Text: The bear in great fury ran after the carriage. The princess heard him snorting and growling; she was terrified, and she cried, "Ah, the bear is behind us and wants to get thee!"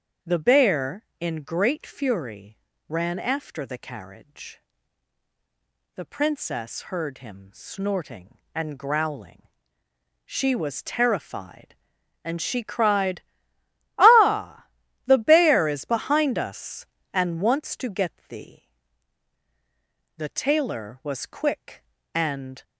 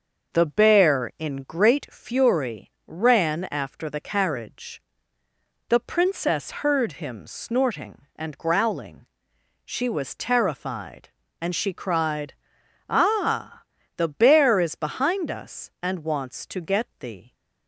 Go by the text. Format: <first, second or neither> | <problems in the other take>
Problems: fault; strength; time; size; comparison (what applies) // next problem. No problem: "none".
second | starts louder than the rest; strong; until 1.4 s; 7 dB; also in the second // pauses between "fury" and "ran"; slight; at 2.5 s; 0.28 s long // goes on to say "The tailor was quick and"; strong; from 20.1 s on; 2.4 s long